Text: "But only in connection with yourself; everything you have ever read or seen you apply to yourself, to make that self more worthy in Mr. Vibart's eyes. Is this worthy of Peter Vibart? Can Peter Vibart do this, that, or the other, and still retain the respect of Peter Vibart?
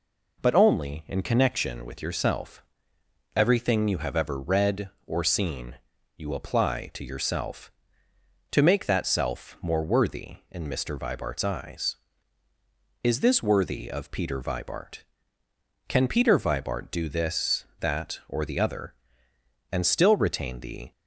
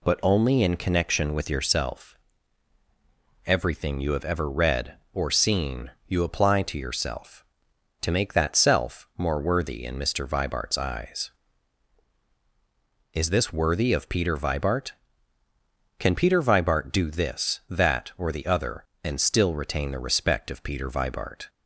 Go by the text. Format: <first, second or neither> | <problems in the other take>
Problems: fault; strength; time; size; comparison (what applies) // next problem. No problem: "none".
second | pauses between "seen" and "you"; at 5.7 s; 0.38 s long; slight in the second // stops before "respect of Peter Vibart"; at 20.9 s